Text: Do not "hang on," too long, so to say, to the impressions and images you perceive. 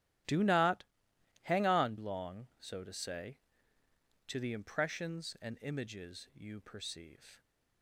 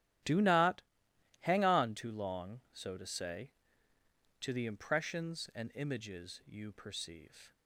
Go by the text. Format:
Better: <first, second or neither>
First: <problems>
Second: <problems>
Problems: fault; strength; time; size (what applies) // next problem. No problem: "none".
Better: second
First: starts louder than the rest; strong; until 1.8 s; 15.5 dB // pauses between "not" and "hang"; noticeable; at 0.8 s; 0.62 s long // skips "too"; at 1.9 s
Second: starts louder than the rest; strong; until 1.8 s; 12 dB // pauses between "not" and "hang"; noticeable; at 0.7 s; 0.62 s long